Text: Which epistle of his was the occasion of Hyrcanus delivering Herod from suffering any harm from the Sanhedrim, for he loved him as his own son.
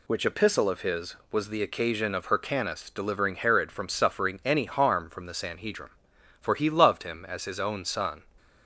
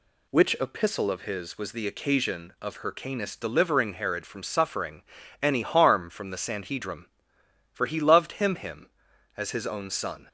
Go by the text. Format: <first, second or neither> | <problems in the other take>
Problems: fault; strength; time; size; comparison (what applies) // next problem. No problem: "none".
first | pauses between "suffering" and "any"; at 5.0 s; 0.40 s long // says "him" twice; at 8.5 s